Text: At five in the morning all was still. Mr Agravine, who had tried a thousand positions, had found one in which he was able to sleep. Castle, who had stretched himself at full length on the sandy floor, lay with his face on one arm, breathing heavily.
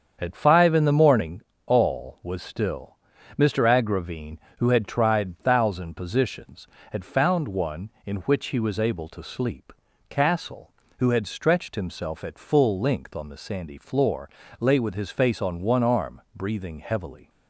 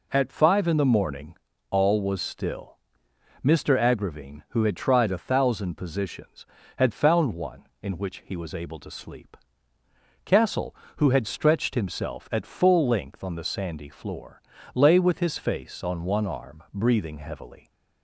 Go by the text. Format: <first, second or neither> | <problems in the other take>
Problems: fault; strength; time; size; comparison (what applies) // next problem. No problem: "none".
second | starts louder than the rest; strong; until 1.1 s; 7.5 dB // pauses between "morning" and "all"; slight; at 1.4 s; 0.26 s long; slight in the second // skips "a"; at 5.4 s